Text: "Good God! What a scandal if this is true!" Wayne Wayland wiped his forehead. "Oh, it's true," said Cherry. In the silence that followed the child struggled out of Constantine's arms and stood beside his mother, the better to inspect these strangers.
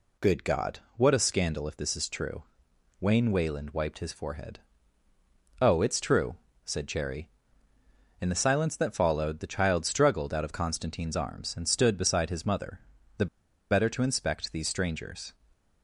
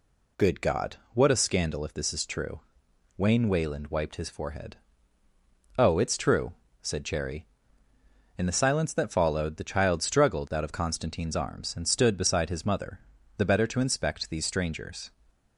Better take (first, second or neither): second